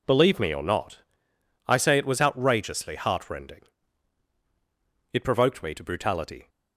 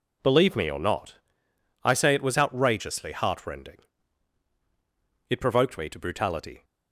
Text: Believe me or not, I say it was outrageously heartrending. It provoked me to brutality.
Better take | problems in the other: neither | none

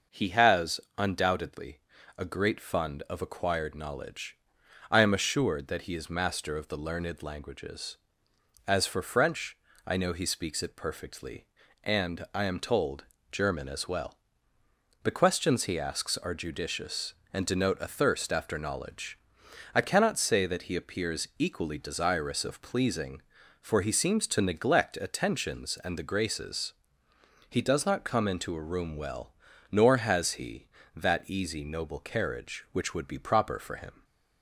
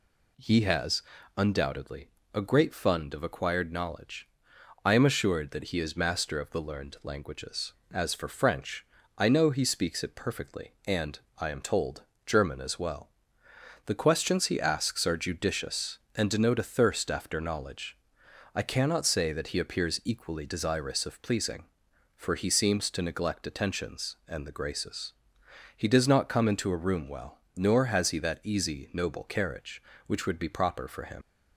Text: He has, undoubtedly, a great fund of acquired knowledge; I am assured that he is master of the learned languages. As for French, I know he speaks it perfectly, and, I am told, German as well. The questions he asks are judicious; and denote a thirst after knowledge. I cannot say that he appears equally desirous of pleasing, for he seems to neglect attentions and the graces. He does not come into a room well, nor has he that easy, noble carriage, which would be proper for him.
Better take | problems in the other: first | leaves "him" unfinished; at 31.2 s; 90 ms

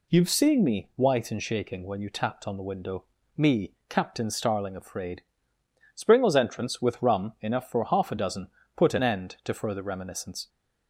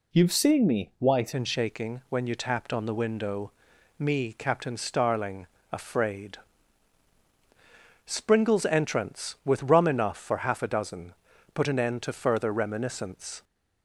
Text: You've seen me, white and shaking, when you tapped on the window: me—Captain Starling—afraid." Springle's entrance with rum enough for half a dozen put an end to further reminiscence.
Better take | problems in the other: first | changes voice at "and"; from 1.3 s on; 12.1 s long // pauses between "dozen" and "put"; at 11.1 s; 0.42 s long; slight in the first

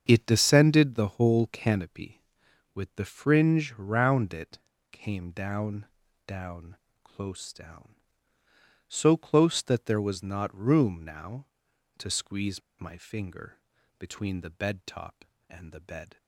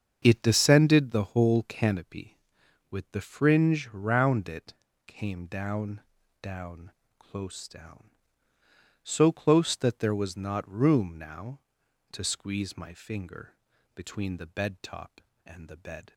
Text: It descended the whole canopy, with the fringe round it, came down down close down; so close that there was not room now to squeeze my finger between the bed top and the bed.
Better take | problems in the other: second | starts louder than the rest; strong; until 1.0 s; 7.5 dB; strong in the second // pauses between "down" and "down"; at 5.8 s; 0.42 s long; also in the second // pauses between "down" and "close"; slight; at 6.7 s; 0.26 s long; slight in the second // pauses between "squeeze" and "my"; slight; at 12.6 s; 0.19 s long // pauses between "finger" and "between"; at 13.5 s; 0.40 s long; also in the second

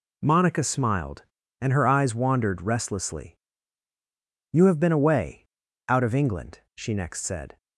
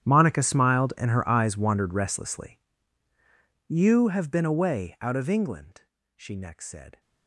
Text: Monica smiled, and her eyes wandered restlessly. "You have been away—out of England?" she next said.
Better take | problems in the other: first | gets quieter; strong; throughout; 19.5 dB

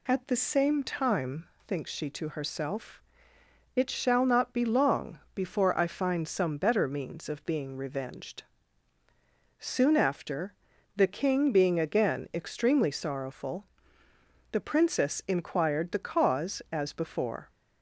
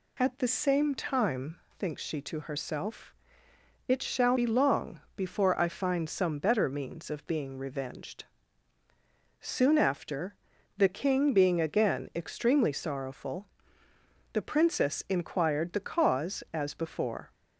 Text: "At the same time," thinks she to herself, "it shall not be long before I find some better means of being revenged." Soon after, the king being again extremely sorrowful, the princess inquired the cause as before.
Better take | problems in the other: first | skips "not"; at 4.3 s // pauses between "long" and "before"; slight; at 4.9 s; 0.16 s long; slight in the first

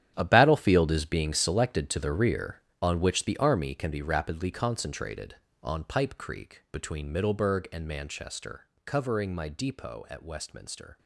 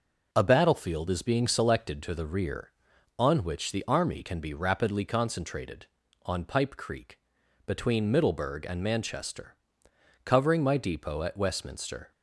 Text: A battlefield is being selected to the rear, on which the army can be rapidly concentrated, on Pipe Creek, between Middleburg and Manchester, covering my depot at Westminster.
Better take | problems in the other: second | gets quieter; strong; throughout; 13 dB

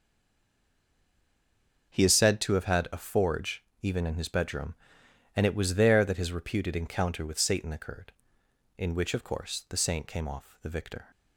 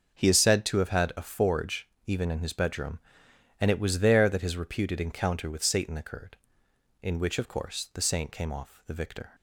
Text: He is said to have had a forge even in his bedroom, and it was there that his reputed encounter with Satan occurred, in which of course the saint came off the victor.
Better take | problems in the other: second | stays silent before the first word; noticeable; until 1.9 s; 1.9 s long // starts louder than the rest; noticeable; until 2.9 s; 6 dB; noticeable in the second // pauses between "forge" and "even"; slight; at 3.6 s; 0.20 s long; slight in the second

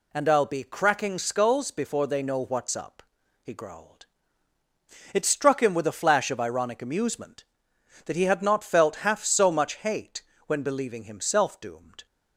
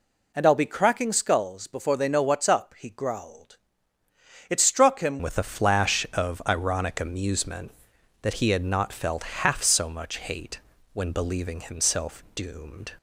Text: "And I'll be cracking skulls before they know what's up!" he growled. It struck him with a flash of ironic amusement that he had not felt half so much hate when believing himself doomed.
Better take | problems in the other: first | changes voice at "with"; from 5.2 s on; 7.7 s long // pauses between "hate" and "when"; slight; at 10.5 s; 0.36 s long; slight in the first

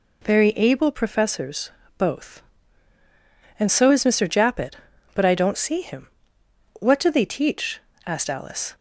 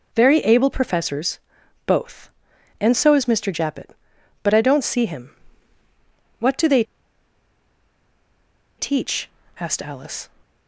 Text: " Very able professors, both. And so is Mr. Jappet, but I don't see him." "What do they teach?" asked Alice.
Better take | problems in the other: first | pauses between "they" and "teach"; strong; at 6.8 s; 1.9 s long

